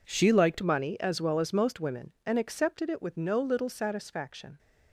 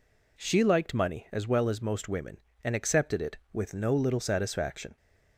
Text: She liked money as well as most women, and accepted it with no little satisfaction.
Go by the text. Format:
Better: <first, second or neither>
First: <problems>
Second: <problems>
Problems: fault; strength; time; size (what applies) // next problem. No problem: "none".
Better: second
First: changes voice at "money"; from 0.6 s on; 3.9 s long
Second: none